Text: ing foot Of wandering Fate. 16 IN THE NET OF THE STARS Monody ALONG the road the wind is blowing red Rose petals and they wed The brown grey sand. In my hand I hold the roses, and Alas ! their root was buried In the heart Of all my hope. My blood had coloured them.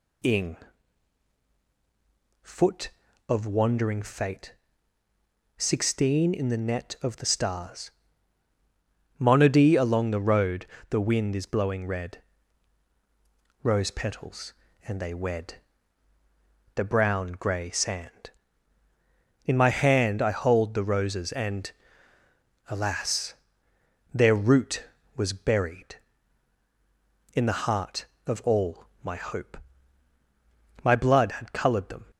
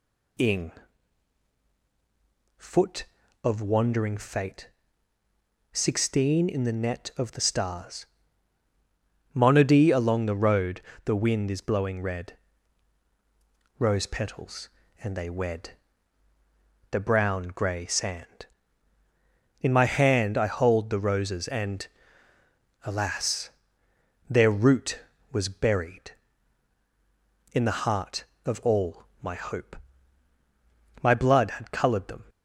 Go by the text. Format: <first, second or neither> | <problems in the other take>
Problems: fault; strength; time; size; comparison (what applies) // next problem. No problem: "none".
neither | pauses between "ing" and "foot"; strong; the same in both // pauses between "STARS" and "Monody"; strong; the same in both // pauses between "road" and "the"; slight; the same in both // pauses between "red" and "Rose"; strong; the same in both // pauses between "wed" and "The"; the same in both // pauses between "and" and "Alas"; noticeable; the same in both // pauses between "all" and "my"; slight; the same in both